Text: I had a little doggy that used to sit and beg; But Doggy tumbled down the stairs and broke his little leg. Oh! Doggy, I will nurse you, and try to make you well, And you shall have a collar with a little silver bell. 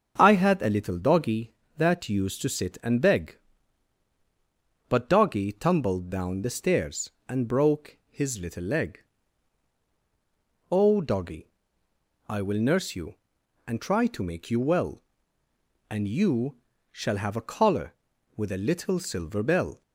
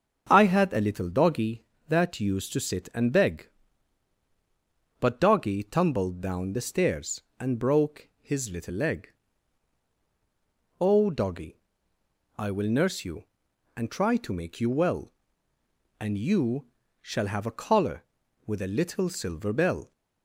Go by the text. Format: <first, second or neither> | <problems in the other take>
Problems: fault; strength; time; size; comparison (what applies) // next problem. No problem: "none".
neither | starts louder than the rest; the same in both // pauses between "you" and "shall"; the same in both